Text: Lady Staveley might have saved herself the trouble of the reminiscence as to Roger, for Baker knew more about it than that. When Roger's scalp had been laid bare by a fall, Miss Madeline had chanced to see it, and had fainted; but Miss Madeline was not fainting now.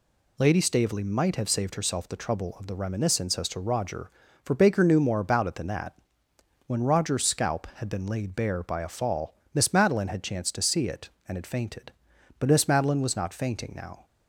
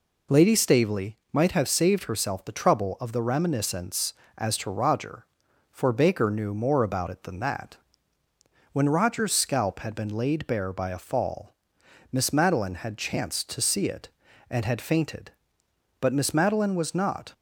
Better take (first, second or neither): first